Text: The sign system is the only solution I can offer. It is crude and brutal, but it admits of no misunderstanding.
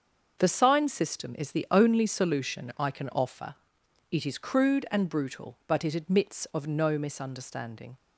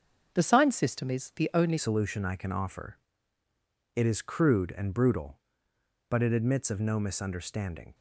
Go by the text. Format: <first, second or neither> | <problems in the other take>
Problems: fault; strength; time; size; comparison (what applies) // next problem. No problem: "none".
first | starts louder than the rest; until 1.4 s; 7 dB; also in the first // changes voice at "solution"; from 1.7 s on; 6.2 s long